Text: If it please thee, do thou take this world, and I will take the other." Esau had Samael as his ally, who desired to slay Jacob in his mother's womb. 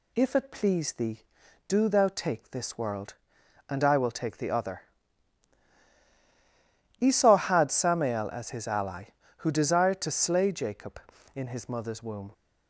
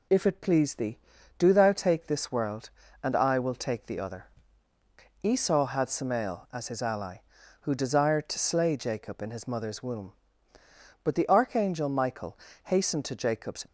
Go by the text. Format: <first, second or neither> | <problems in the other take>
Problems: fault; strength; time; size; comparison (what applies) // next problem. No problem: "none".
first | goes on to say "But the archangel Michael hastened to Jacob's"; strong; from 11.0 s on; 2.6 s long